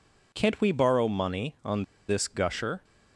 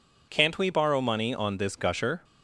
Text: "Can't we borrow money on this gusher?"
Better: second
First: pauses between "on" and "this"; slight; at 1.8 s; 0.26 s long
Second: none

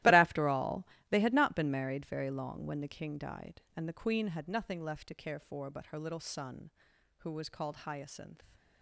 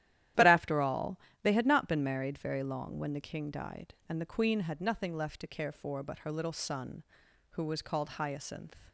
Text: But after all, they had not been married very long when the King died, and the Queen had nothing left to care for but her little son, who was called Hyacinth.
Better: second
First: gets quieter; strong; throughout; 15 dB // starts louder than the rest; strong; until 1.2 s; 15.5 dB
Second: starts louder than the rest; strong; until 1.6 s; 12.5 dB

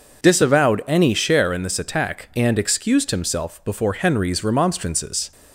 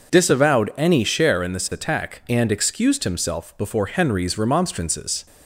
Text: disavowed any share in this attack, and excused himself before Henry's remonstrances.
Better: neither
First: none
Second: none

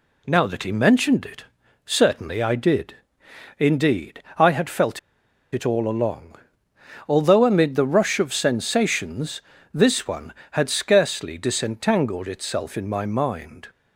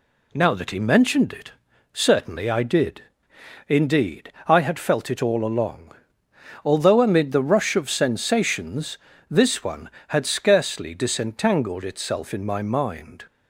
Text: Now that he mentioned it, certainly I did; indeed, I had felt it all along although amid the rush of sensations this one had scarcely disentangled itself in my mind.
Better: second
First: pauses between "felt" and "it"; noticeable; at 4.9 s; 0.55 s long // pauses between "along" and "although"; noticeable; at 6.3 s; 0.74 s long // pauses between "sensations" and "this"; slight; at 9.4 s; 0.32 s long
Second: pauses between "along" and "although"; noticeable; at 5.9 s; 0.74 s long // pauses between "sensations" and "this"; slight; at 8.9 s; 0.32 s long

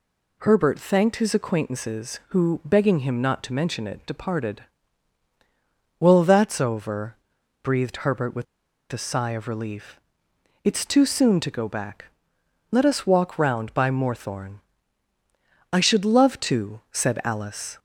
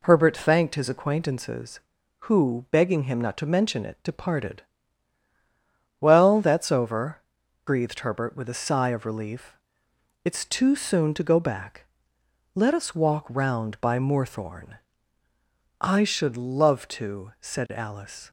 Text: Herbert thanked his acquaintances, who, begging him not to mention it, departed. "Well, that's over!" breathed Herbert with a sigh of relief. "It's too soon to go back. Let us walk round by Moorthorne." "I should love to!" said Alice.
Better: second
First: pauses between "with" and "a"; noticeable; at 8.4 s; 0.47 s long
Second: none

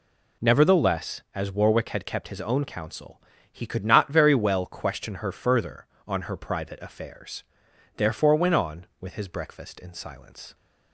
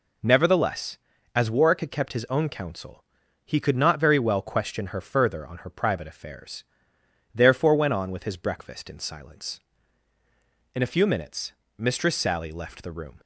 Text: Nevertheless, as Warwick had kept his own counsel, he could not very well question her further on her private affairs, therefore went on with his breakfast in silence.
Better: first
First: none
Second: goes on to say "In a few minutes Mistress Sally left the room"; strong; from 10.7 s on; 2.4 s long

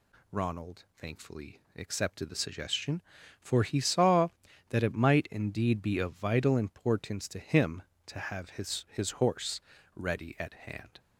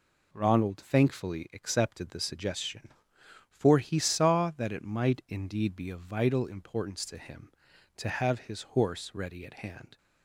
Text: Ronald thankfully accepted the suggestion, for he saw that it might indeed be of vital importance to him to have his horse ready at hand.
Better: second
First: pauses between "Ronald" and "thankfully"; slight; at 0.8 s; 0.16 s long // pauses between "thankfully" and "accepted"; slight; at 1.5 s; 0.18 s long // says "his" twice; at 8.9 s // pauses between "horse" and "ready"; slight; at 9.6 s; 0.34 s long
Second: none

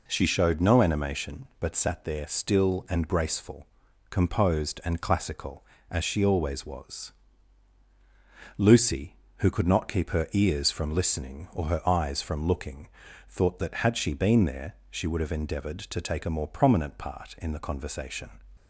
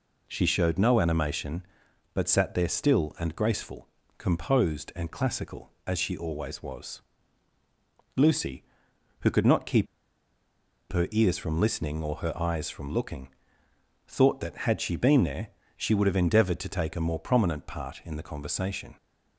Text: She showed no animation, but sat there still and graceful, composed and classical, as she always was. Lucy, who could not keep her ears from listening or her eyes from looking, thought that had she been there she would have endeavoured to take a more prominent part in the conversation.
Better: first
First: pauses between "there" and "she"; slight; at 14.7 s; 0.16 s long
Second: pauses between "keep" and "her"; at 9.8 s; 1.0 s long // pauses between "there" and "she"; slight; at 15.4 s; 0.28 s long

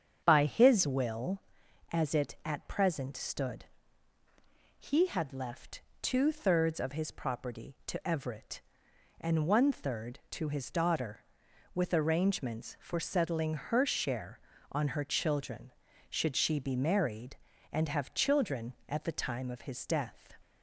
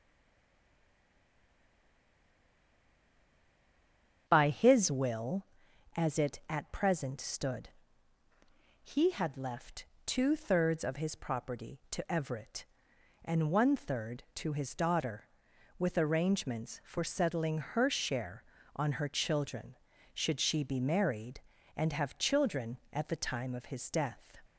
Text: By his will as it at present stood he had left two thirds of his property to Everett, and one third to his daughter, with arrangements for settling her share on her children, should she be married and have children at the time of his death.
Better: first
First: starts louder than the rest; strong; until 1.2 s; 7.5 dB // pauses between "stood" and "he"; at 3.6 s; 1.1 s long // pauses between "left" and "two"; slight; at 5.8 s; 0.20 s long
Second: stays silent before the first word; strong; until 4.2 s; 4.2 s long // starts louder than the rest; strong; until 5.2 s; 7.5 dB // pauses between "stood" and "he"; at 7.6 s; 1.1 s long // pauses between "left" and "two"; slight; at 9.8 s; 0.20 s long

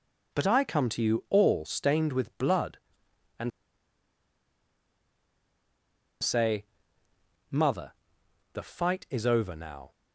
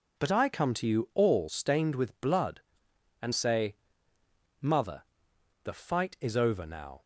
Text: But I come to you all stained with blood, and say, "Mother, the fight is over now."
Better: second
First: pauses between "and" and "say"; strong; at 3.5 s; 2.7 s long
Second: none

